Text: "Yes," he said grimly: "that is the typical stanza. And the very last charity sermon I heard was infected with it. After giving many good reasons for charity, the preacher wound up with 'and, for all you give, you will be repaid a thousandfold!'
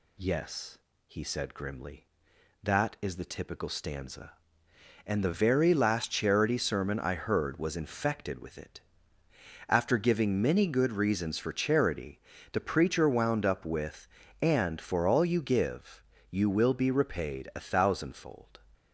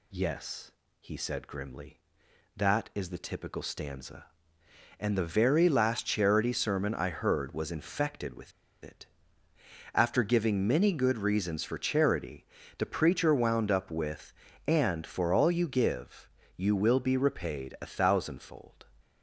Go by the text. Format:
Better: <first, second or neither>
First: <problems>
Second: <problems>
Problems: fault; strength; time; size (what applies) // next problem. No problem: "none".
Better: first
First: none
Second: pauses between "with" and "it"; slight; at 8.5 s; 0.31 s long